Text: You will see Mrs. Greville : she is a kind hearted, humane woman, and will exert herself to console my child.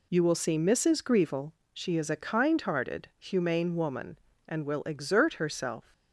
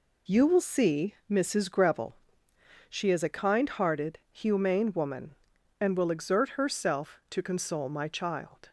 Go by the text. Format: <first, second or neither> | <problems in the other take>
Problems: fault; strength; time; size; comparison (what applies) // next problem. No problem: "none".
second | stops before "to console my child"; at 5.9 s